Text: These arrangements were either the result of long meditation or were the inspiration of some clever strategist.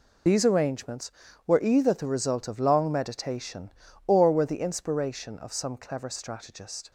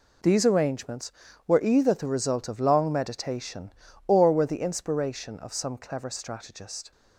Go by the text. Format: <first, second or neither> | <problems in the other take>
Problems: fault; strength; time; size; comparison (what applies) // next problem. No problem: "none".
second | loses the start of "These"; at 0.2 s; 35 ms